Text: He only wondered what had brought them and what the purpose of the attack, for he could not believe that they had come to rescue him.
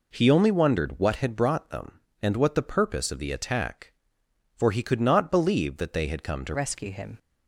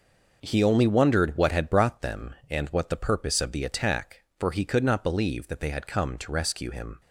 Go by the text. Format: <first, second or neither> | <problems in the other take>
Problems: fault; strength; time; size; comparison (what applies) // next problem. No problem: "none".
second | changes voice at "rescue"; from 6.5 s on; 0.6 s long